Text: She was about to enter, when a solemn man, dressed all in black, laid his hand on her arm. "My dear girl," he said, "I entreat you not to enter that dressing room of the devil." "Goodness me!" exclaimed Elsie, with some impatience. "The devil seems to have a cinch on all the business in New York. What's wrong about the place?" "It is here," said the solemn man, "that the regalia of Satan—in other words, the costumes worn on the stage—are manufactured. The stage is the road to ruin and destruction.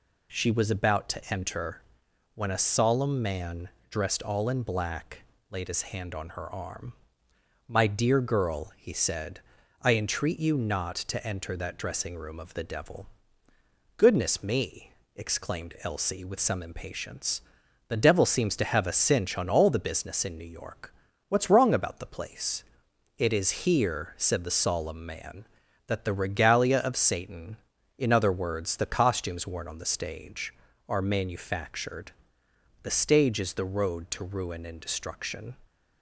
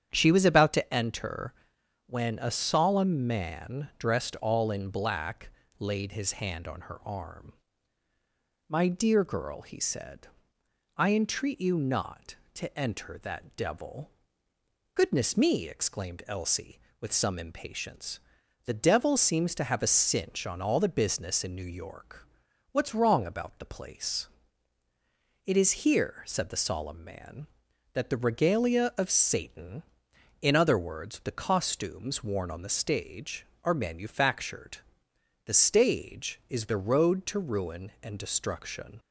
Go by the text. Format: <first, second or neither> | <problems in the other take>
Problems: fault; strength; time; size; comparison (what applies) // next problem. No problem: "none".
first | starts louder than the rest; strong; until 1.1 s; 9 dB // skips "dressing room of the"; at 13.5 s